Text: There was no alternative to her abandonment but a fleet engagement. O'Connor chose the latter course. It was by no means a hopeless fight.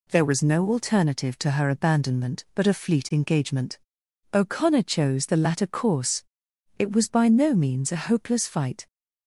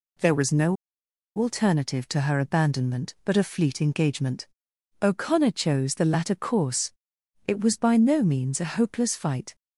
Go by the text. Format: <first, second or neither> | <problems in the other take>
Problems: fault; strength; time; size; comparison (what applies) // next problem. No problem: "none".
first | pauses between "no" and "alternative"; noticeable; at 0.7 s; 0.63 s long